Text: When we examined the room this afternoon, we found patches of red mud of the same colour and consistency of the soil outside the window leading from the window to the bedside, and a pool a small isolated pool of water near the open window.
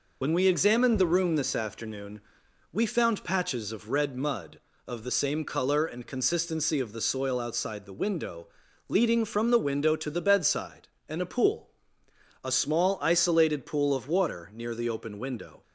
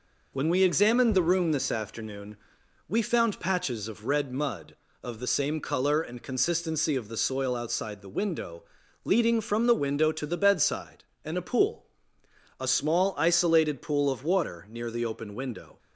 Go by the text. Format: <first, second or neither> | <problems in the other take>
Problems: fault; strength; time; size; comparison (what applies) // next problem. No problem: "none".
second | loses the start of "When"; at 0.2 s; 30 ms // pauses between "window" and "leading"; at 8.4 s; 0.40 s long; also in the second // pauses between "pool" and "a"; noticeable; at 11.6 s; 0.74 s long; noticeable in the second